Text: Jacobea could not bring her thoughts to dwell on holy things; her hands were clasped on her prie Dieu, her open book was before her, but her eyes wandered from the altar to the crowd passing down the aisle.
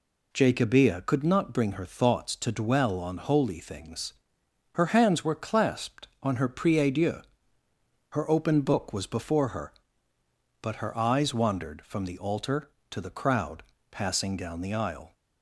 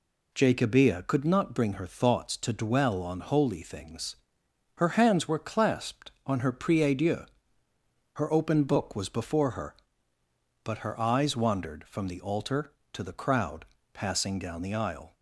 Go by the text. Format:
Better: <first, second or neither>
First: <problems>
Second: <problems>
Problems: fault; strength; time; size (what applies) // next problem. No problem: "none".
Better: neither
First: pauses between "crowd" and "passing"; slight; at 13.6 s; 0.28 s long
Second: pauses between "crowd" and "passing"; slight; at 13.6 s; 0.28 s long